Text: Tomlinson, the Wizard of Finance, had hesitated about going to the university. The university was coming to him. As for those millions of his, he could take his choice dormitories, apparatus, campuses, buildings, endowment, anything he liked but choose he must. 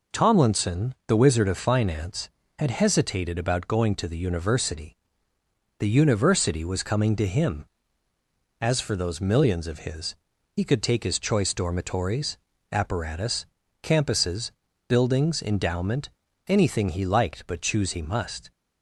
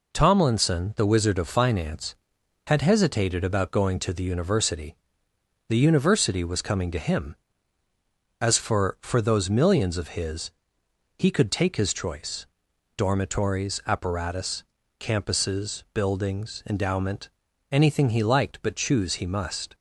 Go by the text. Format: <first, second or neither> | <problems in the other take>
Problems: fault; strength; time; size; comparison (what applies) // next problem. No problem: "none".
first | says "for" twice; at 9.0 s // pauses between "choice" and "dormitories"; noticeable; at 12.4 s; 0.50 s long